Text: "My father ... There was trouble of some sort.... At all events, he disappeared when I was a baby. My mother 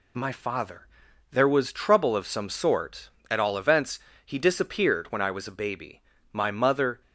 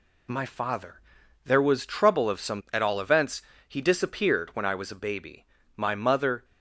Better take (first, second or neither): first